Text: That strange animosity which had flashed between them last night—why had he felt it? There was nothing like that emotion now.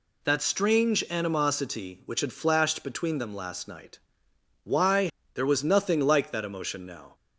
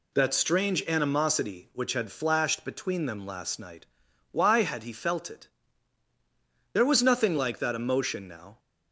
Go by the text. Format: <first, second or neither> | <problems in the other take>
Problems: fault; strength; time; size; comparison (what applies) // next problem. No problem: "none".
second | skips "had he felt it"; at 5.2 s